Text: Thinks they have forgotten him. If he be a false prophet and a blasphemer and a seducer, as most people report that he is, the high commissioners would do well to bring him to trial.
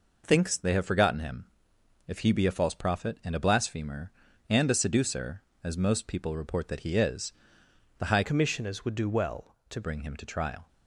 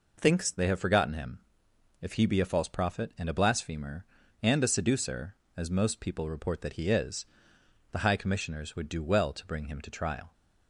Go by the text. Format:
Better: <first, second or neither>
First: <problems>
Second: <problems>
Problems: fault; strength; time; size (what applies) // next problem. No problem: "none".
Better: second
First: changes voice from "commissioners" to "to"; from 8.2 to 9.8 s; 1.6 s long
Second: none